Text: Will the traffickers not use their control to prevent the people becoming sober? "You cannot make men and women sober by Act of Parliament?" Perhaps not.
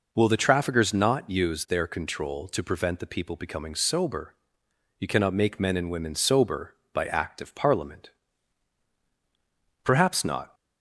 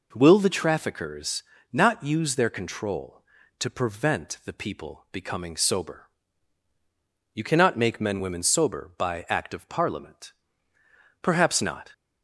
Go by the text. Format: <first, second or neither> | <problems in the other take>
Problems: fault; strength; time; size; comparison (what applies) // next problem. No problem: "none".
first | pauses between "traffickers" and "not"; slight; at 1.4 s; 0.28 s long // skips "and"; at 8.1 s